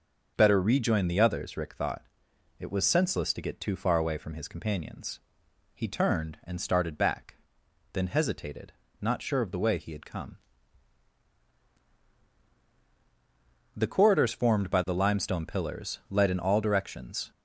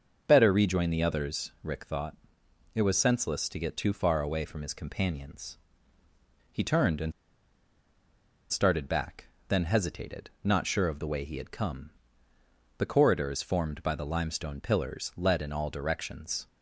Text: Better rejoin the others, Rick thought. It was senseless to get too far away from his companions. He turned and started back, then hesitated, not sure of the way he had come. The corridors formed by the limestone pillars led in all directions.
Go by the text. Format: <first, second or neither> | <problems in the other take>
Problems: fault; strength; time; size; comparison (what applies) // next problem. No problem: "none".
first | starts louder than the rest; until 1.2 s; 6.5 dB; also in the first // pauses between "and" and "started"; strong; at 7.1 s; 1.3 s long